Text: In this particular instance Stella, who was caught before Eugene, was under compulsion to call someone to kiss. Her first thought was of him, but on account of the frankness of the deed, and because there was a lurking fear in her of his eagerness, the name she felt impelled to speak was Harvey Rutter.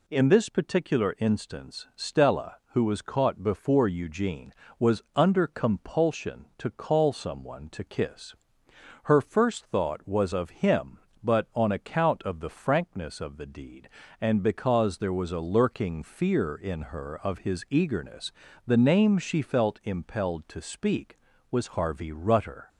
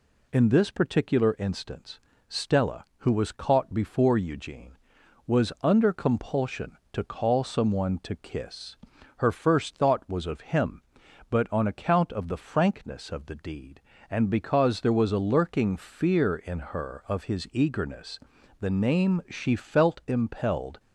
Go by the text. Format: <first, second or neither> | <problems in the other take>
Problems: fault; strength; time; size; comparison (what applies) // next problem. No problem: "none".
first | pauses between "instance" and "Stella"; slight; at 1.9 s; 0.30 s long // stops before "to speak was Harvey Rutter"; at 20.7 s